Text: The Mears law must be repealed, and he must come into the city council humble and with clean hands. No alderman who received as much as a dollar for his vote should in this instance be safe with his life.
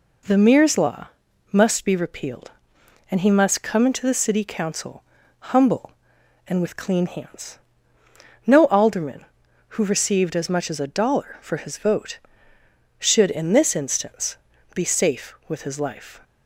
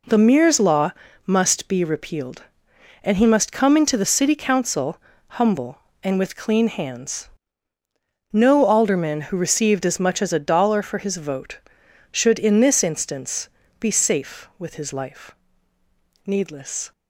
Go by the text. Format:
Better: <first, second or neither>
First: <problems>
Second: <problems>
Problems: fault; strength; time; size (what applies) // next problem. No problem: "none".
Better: first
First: pauses between "law" and "must"; at 1.0 s; 0.42 s long // pauses between "council" and "humble"; noticeable; at 5.0 s; 0.48 s long // pauses between "instance" and "be"; slight; at 14.3 s; 0.36 s long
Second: pauses between "law" and "must"; slight; at 0.9 s; 0.34 s long // pauses between "council" and "humble"; at 4.9 s; 0.42 s long // pauses between "instance" and "be"; slight; at 13.4 s; 0.32 s long // goes on to say "Needless"; noticeable; from 16.2 s on; 0.66 s long